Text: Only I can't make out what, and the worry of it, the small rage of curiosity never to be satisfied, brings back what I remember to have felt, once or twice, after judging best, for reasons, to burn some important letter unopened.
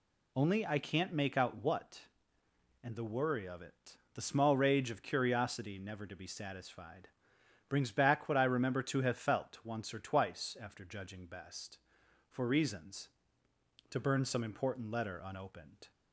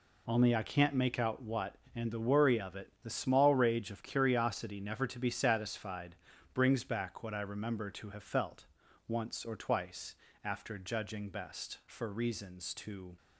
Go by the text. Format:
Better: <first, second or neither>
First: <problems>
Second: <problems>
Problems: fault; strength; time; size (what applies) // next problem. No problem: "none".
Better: first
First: none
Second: stops before "burn some important letter unopened"; at 13.1 s